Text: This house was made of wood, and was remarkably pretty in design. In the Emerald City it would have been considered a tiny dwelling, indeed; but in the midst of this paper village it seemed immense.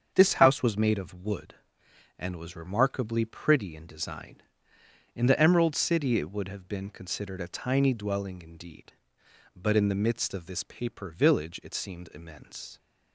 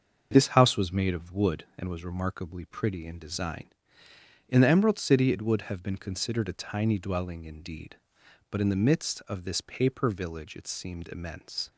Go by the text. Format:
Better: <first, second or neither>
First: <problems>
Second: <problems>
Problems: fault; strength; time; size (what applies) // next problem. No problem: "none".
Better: neither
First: starts louder than the rest; strong; until 1.1 s; 7 dB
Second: starts louder than the rest; until 1.3 s; 6.5 dB